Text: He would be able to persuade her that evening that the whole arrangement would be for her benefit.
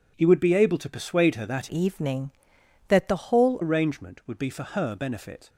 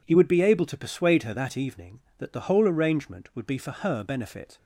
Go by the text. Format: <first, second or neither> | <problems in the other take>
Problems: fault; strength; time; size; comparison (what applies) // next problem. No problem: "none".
second | changes voice from "evening" to "whole"; from 1.6 to 3.5 s; 1.9 s long